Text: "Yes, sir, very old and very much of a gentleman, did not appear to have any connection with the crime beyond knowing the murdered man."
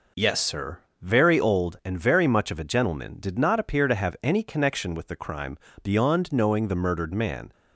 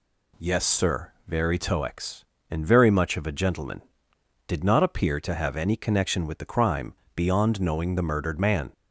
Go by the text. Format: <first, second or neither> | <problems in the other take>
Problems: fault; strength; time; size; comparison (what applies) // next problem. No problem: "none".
first | says "toex" for "old"; at 1.5 s // pauses between "crime" and "beyond"; slight; at 6.9 s; 0.20 s long; slight in the first